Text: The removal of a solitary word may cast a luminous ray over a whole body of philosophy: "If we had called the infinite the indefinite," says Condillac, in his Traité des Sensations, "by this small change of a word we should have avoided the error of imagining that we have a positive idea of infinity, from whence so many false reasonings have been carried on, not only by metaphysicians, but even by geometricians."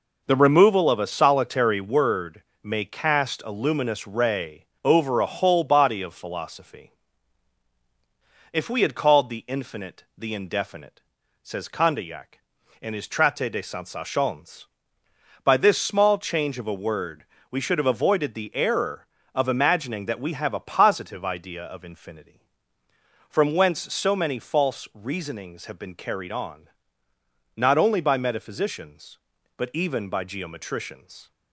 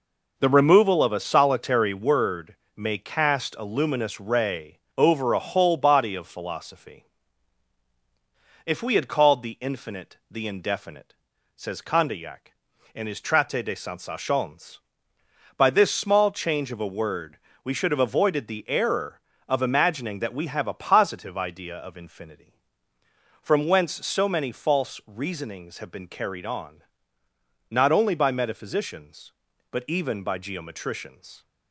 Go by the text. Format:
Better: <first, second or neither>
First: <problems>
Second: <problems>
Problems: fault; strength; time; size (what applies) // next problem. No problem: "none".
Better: neither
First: pauses between "word" and "may"; slight; at 2.4 s; 0.20 s long // pauses between "ray" and "over"; slight; at 4.6 s; 0.18 s long // pauses between "word" and "we"; slight; at 17.2 s; 0.26 s long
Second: pauses between "word" and "may"; slight; at 2.5 s; 0.20 s long // pauses between "ray" and "over"; slight; at 4.7 s; 0.18 s long // pauses between "word" and "we"; slight; at 17.3 s; 0.26 s long